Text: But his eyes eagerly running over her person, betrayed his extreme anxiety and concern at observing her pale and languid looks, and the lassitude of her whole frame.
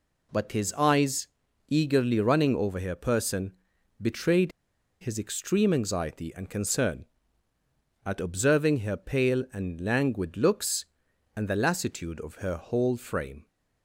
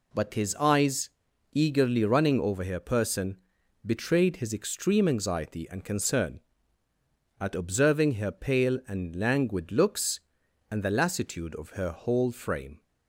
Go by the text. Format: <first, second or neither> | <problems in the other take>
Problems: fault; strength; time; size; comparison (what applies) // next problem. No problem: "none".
second | pauses between "eyes" and "eagerly"; at 1.2 s; 0.40 s long; also in the second // pauses between "betrayed" and "his"; noticeable; at 4.5 s; 0.50 s long